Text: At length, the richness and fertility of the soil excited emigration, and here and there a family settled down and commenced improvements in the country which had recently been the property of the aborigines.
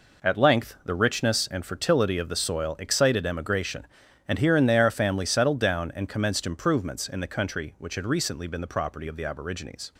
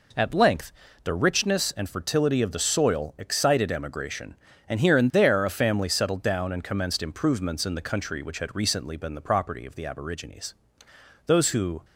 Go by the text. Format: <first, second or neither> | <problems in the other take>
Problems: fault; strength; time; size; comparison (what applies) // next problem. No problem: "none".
first | goes on to say "Those who"; from 11.2 s on; 0.58 s long